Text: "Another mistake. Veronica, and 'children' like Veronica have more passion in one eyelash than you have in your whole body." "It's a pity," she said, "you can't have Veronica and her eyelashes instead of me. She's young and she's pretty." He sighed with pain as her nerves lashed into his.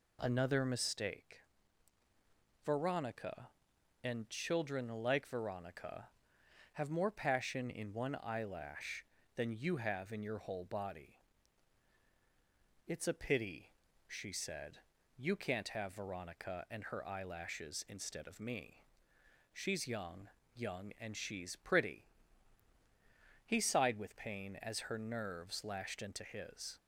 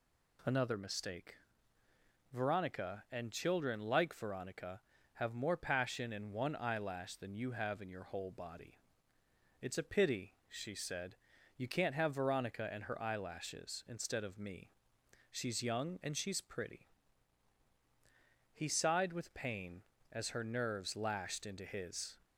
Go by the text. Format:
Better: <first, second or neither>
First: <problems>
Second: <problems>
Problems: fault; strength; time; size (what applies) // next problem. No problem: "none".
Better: second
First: says "young" twice; at 20.5 s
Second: none